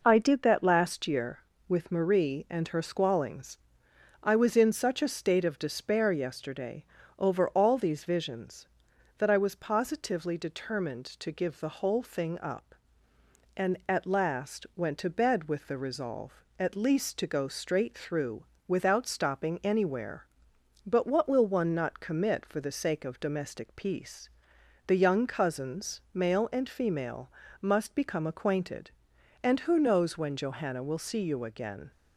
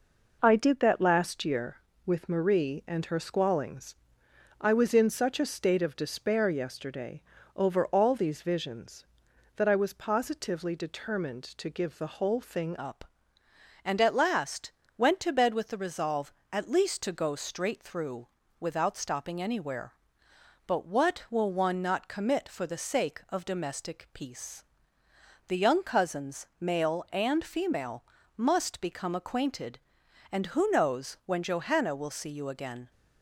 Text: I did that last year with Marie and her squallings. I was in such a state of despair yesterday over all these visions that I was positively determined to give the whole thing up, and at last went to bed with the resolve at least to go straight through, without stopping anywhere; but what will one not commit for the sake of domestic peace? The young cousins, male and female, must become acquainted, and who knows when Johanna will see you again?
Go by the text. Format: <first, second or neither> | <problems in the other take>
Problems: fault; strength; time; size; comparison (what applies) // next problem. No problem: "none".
first | pauses between "yesterday" and "over"; slight; at 7.2 s; 0.36 s long; slight in the first // changes voice at "up"; from 12.7 s on; 20.2 s long // pauses between "last" and "went"; slight; at 14.7 s; 0.26 s long